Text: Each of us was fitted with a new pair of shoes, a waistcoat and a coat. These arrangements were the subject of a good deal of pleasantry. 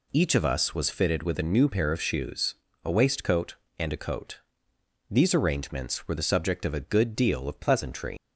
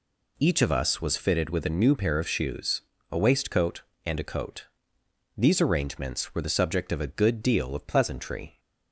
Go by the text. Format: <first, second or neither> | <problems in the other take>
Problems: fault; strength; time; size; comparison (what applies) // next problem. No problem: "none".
second | leaves "pleasantry" unfinished; at 8.1 s; 155 ms